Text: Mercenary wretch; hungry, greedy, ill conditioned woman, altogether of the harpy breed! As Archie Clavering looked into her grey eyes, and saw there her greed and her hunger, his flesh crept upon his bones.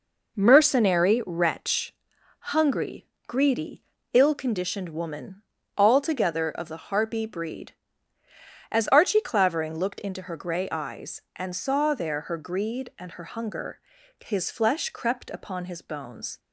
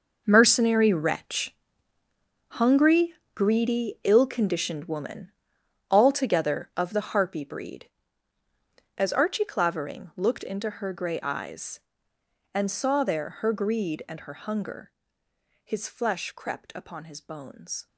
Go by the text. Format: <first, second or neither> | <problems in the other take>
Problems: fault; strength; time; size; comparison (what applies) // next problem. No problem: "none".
first | gets quieter; strong; throughout; 12.5 dB